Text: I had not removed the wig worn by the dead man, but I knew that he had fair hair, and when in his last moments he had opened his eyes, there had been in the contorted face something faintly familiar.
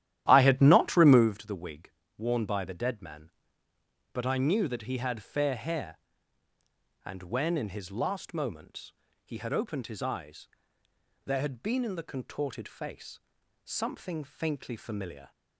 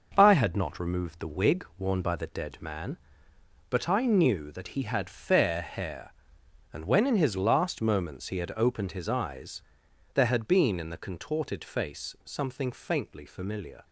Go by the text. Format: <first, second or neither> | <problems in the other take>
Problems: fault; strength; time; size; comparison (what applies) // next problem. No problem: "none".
second | starts louder than the rest; strong; until 1.3 s; 12 dB // pauses between "wig" and "worn"; slight; at 1.9 s; 0.26 s long // pauses between "moments" and "he"; slight; at 8.9 s; 0.32 s long // pauses between "face" and "something"; at 13.1 s; 0.44 s long